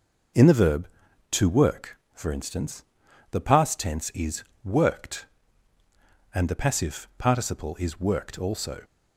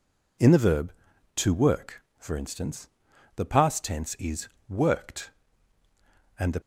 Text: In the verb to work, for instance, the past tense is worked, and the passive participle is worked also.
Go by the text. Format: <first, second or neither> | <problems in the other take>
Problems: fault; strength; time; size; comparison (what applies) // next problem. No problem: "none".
first | pauses between "is" and "worked"; slight; at 4.4 s; 0.22 s long; slight in the first // stops before "passive participle is worked also"; at 6.6 s